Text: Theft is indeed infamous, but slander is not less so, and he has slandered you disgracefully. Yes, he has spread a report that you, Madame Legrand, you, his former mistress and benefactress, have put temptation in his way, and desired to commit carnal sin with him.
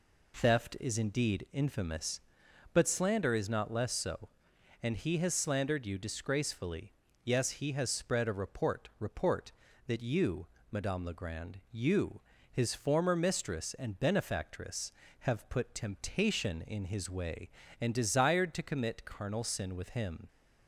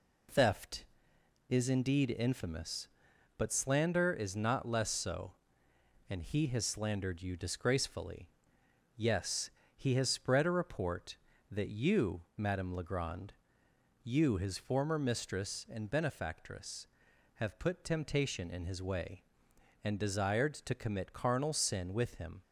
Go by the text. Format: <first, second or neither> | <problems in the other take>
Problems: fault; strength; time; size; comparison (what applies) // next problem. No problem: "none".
second | says "report" twice; at 8.9 s